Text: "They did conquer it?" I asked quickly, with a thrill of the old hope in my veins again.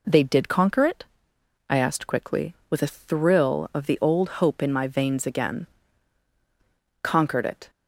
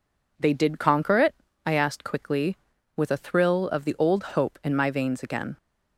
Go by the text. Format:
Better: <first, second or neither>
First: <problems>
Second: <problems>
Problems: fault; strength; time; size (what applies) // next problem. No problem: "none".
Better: second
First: goes on to say "Conquered it"; noticeable; from 7.0 s on; 0.68 s long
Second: none